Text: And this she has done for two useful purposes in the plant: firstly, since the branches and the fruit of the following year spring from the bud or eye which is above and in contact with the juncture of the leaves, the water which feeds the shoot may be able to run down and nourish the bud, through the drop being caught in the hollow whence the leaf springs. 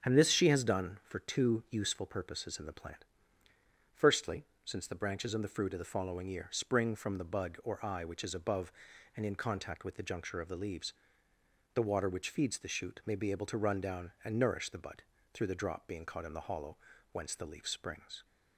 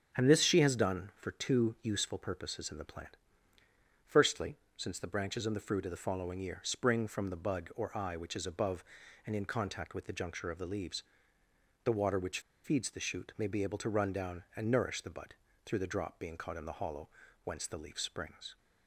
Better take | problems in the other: first | starts louder than the rest; until 1.2 s; 6 dB; also in the first // pauses between "which" and "feeds"; slight; at 12.4 s; 0.23 s long // pauses between "hollow" and "whence"; slight; at 17.0 s; 0.36 s long; slight in the first

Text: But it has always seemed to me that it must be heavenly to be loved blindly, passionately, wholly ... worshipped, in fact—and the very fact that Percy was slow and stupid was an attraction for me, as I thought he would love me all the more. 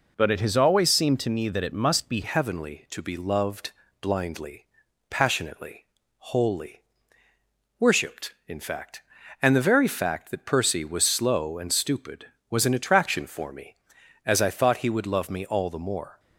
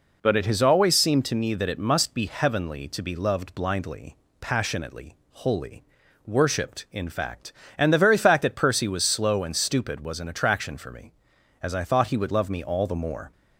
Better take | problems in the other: second | changes voice at "heavenly"; from 2.2 s on; 13.9 s long // pauses between "loved" and "blindly"; slight; at 3.7 s; 0.28 s long

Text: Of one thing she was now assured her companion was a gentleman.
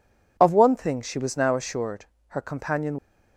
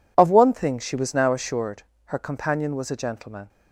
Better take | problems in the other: second | pauses between "assured" and "her"; slight; at 2.0 s; 0.22 s long; slight in the second // stops before "was a gentleman"; at 2.9 s

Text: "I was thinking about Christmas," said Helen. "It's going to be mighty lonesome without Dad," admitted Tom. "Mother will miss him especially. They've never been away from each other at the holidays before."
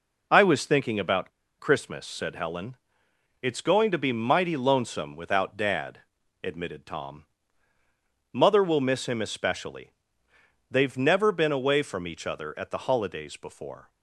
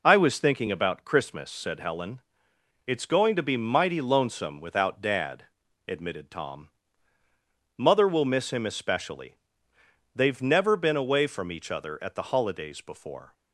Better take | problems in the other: second | pauses between "about" and "Christmas"; slight; at 1.3 s; 0.28 s long

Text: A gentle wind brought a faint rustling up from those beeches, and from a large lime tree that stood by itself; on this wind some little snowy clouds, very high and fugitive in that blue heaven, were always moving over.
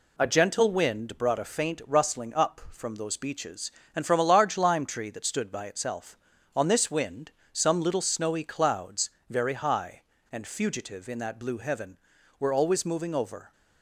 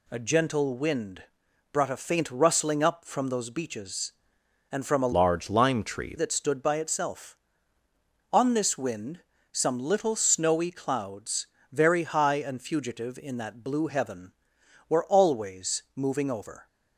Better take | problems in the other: first | pauses between "wind" and "brought"; noticeable; at 1.2 s; 0.48 s long // changes voice from "large" to "tree"; from 5.1 to 6.1 s; 1.0 s long // pauses between "wind" and "some"; slight; at 9.2 s; 0.32 s long; slight in the first

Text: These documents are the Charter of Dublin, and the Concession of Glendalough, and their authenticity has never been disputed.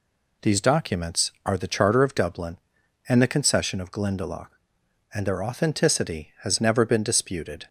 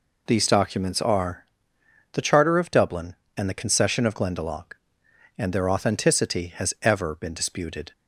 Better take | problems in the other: first | pauses between "are" and "the"; noticeable; at 1.4 s; 0.68 s long // says "ever" for "never"; at 6.8 s

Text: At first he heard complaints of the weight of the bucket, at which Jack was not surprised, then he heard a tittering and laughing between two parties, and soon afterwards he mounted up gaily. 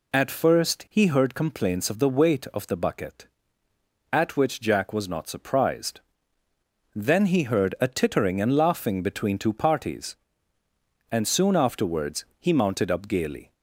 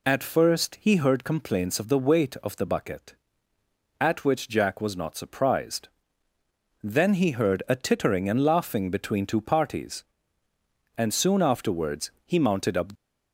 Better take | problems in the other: first | pauses between "afterwards" and "he"; slight; at 12.1 s; 0.16 s long; slight in the first // stops before "gaily"; at 12.9 s

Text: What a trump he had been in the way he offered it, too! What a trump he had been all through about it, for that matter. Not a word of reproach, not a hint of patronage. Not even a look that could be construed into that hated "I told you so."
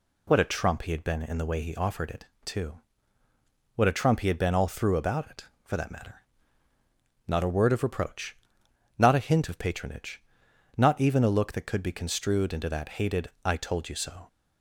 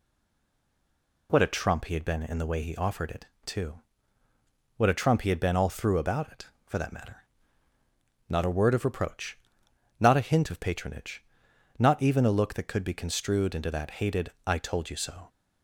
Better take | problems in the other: first | stays silent before the first word; noticeable; until 1.2 s; 1.2 s long // pauses between "hated" and "I"; slight; at 14.3 s; 0.16 s long; slight in the first

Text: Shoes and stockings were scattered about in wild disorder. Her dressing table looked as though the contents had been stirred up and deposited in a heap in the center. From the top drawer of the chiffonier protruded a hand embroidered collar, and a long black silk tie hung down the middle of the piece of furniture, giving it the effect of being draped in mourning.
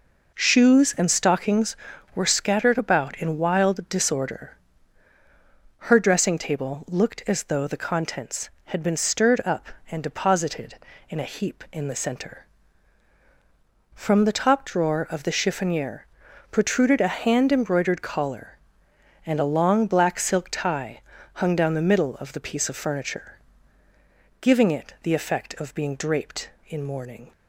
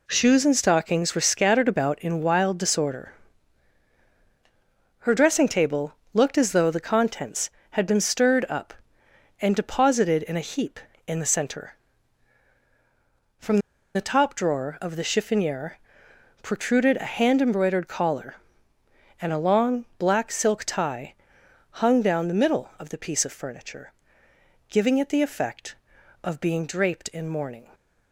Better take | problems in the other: first | pauses between "table" and "looked"; slight; at 5.9 s; 0.20 s long // pauses between "From" and "the"; at 13.5 s; 0.37 s long // pauses between "chiffonier" and "protruded"; noticeable; at 15.7 s; 0.66 s long; also in the first // pauses between "tie" and "hung"; noticeable; at 21.1 s; 0.60 s long; slight in the first

